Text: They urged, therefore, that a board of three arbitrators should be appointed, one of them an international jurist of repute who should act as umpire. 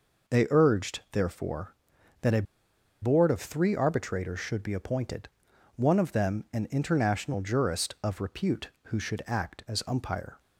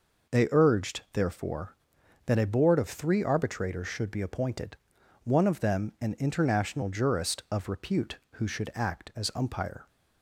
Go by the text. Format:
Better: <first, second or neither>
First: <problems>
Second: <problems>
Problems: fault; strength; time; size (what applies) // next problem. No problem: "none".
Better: second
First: pauses between "a" and "board"; noticeable; at 2.4 s; 0.59 s long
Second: none